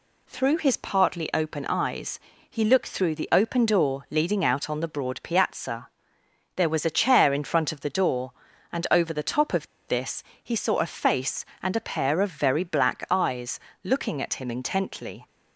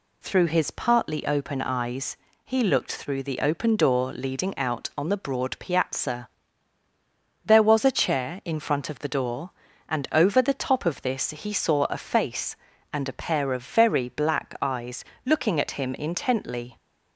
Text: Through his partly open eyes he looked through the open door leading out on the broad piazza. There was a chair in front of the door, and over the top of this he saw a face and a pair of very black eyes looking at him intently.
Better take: second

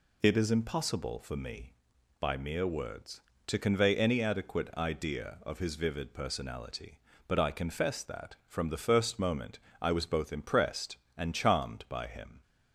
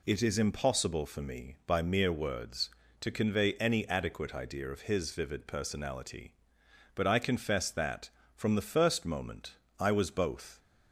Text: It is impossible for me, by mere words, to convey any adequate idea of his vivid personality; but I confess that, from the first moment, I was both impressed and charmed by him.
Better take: first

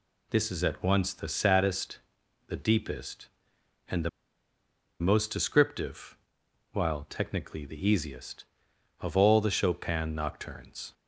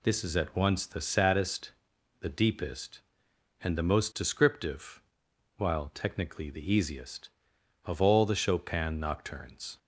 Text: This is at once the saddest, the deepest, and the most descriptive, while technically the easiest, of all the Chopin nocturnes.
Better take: second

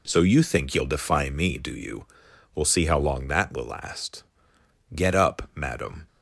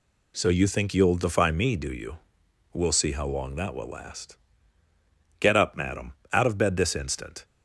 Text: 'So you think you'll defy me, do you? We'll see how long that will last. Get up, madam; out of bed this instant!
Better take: second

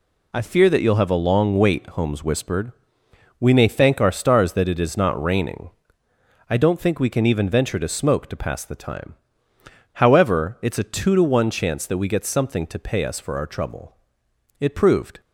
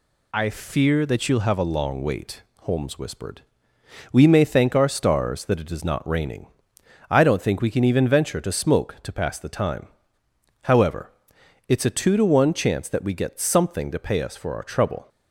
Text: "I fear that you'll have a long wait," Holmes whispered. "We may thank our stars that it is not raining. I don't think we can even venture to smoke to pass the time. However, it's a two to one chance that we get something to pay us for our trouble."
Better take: second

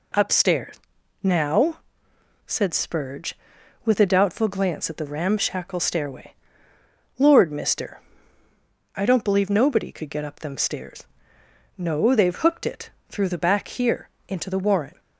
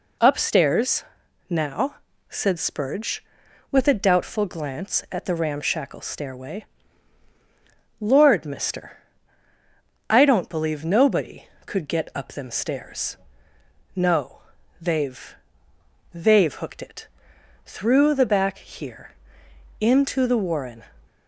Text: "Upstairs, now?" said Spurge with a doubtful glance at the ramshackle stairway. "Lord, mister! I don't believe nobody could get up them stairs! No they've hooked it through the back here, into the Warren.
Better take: first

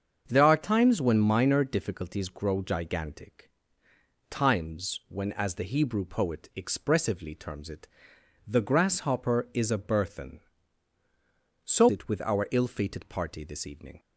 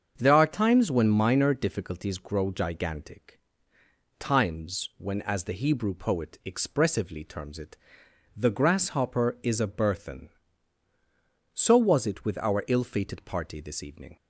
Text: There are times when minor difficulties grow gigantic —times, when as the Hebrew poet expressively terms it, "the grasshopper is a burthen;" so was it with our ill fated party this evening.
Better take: second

